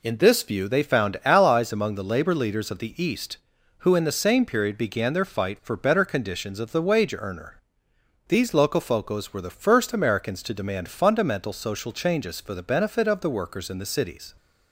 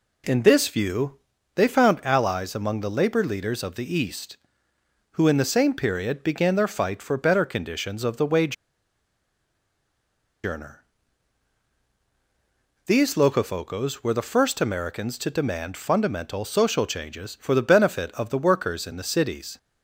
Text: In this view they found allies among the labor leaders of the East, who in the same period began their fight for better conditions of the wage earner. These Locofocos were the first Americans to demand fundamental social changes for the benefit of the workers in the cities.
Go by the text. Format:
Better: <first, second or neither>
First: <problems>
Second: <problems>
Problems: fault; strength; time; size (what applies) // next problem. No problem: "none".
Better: first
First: none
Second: pauses between "view" and "they"; slight; at 1.1 s; 0.36 s long // pauses between "wage" and "earner"; strong; at 8.5 s; 1.9 s long